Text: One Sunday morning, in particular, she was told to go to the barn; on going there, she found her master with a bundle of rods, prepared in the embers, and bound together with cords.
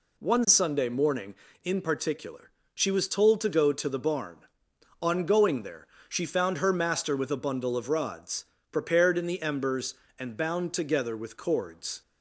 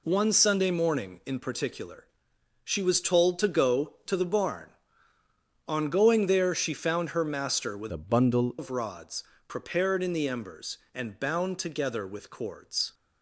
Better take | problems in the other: first | changes voice from "a" to "bundle"; from 7.9 to 8.5 s; 0.6 s long

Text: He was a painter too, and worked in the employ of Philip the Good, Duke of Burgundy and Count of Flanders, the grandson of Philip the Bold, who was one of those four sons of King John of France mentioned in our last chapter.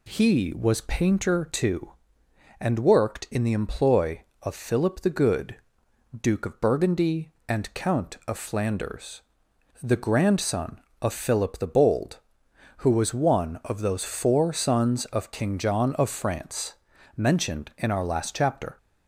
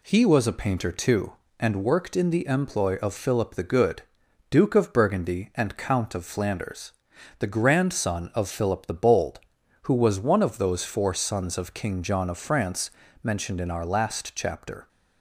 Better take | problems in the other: second | skips "a"; at 0.7 s // pauses between "France" and "mentioned"; at 16.7 s; 0.42 s long; slight in the second

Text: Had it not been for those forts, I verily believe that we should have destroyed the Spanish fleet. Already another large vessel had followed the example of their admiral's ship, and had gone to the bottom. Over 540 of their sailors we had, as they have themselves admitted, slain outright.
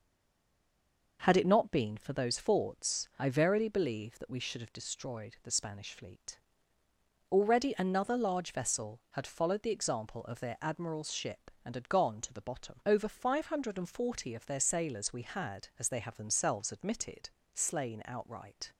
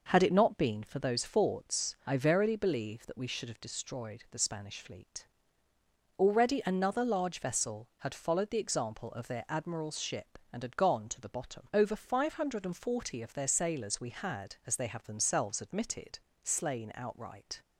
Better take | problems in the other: second | stays silent before the first word; noticeable; until 1.1 s; 1.1 s long

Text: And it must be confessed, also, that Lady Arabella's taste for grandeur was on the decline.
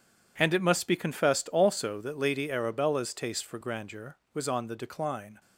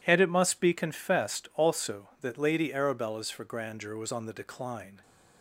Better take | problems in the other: first | skips "taste"; at 3.2 s

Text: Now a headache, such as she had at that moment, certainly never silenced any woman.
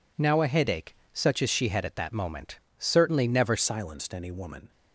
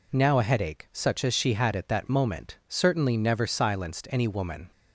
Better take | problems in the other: second | changes voice at "silenced"; from 3.5 s on; 1.2 s long

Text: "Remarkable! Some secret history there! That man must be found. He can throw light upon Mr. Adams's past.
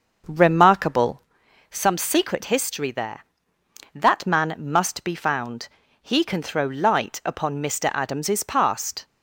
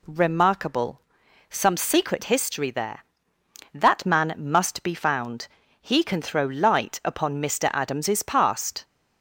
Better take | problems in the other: second | starts louder than the rest; until 1.4 s; 6.5 dB

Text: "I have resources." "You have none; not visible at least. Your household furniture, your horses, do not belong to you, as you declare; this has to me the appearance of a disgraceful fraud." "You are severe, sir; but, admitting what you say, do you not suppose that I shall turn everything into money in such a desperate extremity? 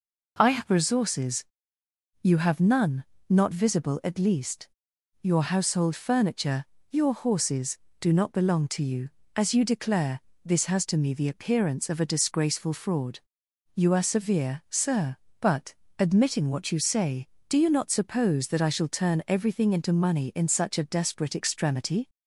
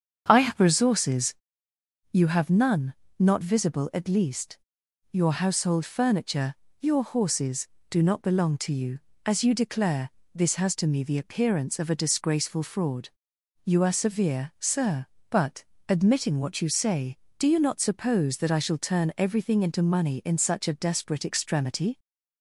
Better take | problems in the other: first | starts louder than the rest; strong; until 1.8 s; 7.5 dB

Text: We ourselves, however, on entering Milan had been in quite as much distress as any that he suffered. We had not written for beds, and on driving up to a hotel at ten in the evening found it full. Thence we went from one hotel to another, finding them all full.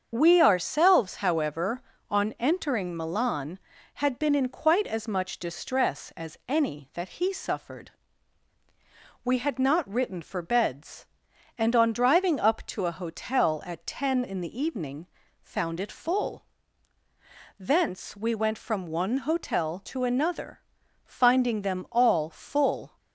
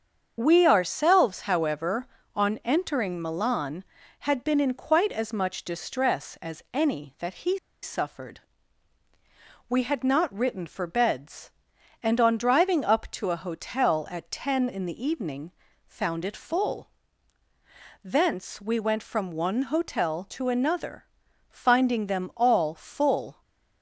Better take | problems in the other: first | starts louder than the rest; strong; until 1.3 s; 7.5 dB; strong in the first // pauses between "he" and "suffered"; slight; at 7.5 s; 0.25 s long // pauses between "evening" and "found"; slight; at 15.5 s; 0.34 s long; slight in the first

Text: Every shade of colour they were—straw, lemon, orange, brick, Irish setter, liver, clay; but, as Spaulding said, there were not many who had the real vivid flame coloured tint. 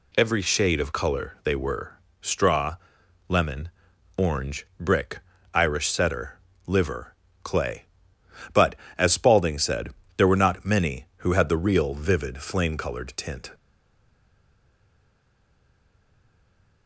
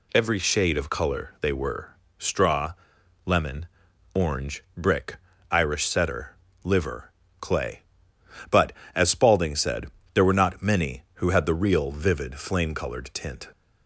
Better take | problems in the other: second | stays silent after the last word; strong; from 13.5 s on; 3.3 s long

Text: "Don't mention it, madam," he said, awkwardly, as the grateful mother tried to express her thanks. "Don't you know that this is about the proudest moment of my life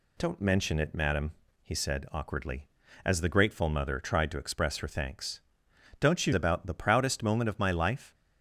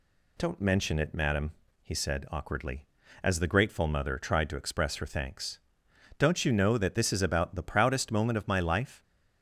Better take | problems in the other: second | skips "know that this is"; at 6.3 s

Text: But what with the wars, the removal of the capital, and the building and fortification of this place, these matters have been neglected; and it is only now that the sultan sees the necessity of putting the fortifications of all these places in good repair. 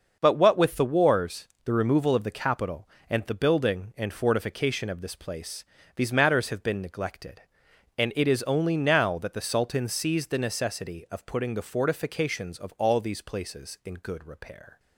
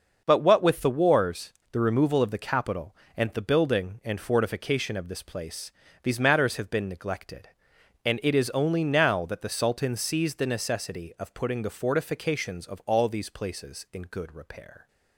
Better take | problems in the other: neither | starts louder than the rest; noticeable; the same in both

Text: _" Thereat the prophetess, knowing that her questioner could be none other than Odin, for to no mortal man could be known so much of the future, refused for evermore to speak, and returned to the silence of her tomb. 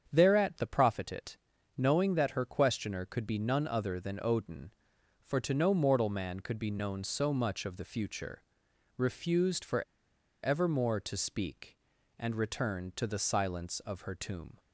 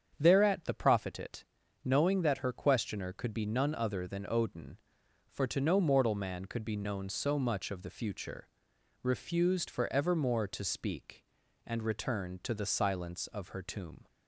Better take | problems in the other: second | starts louder than the rest; strong; until 1.0 s; 7.5 dB; strong in the second // pauses between "for" and "evermore"; noticeable; at 9.8 s; 0.58 s long

